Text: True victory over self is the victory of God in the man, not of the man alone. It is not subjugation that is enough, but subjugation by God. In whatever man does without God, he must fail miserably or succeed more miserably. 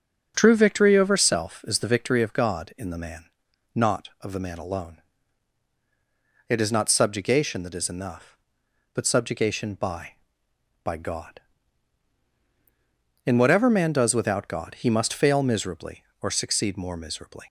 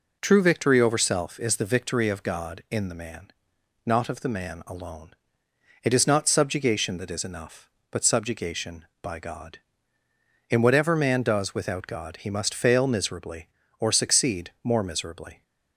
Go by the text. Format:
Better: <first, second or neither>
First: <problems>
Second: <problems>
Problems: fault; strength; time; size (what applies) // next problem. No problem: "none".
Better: second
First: starts louder than the rest; until 1.3 s; 6.5 dB // says "by" twice; at 10.8 s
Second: none